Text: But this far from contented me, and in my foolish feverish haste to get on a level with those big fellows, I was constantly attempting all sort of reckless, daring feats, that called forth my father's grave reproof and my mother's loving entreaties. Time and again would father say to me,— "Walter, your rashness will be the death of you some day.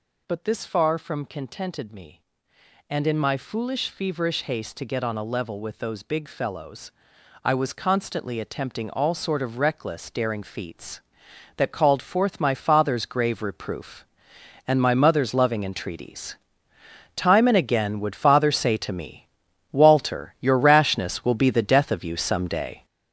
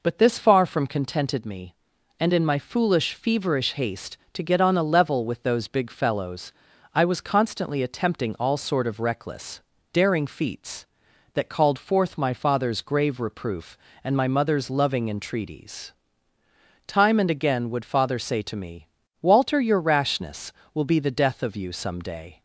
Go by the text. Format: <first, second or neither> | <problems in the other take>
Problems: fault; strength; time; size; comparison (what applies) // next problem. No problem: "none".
second | gets louder; strong; throughout; 7.5 dB